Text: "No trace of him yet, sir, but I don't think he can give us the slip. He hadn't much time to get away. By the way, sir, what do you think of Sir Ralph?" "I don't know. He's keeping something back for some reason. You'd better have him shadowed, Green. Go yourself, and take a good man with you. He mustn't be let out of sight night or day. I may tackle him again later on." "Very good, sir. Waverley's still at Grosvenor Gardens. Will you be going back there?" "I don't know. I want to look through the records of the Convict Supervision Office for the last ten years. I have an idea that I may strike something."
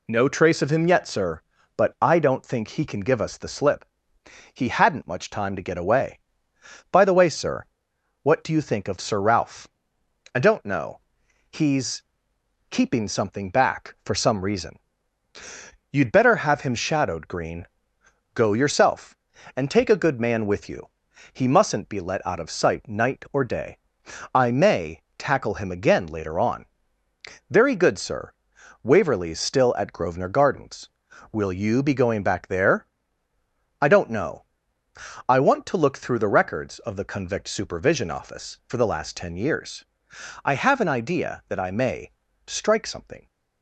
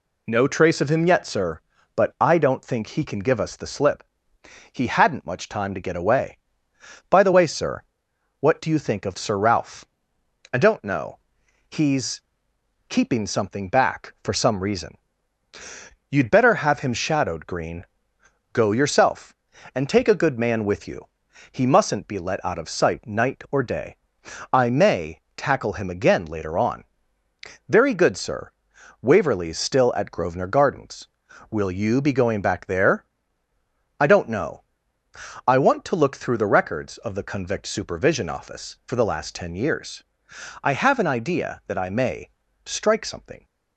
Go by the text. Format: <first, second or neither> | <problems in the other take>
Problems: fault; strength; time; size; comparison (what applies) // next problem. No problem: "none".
neither | pauses between "He's" and "keeping"; noticeable; the same in both // pauses between "may" and "tackle"; slight; the same in both // pauses between "may" and "strike"; slight; the same in both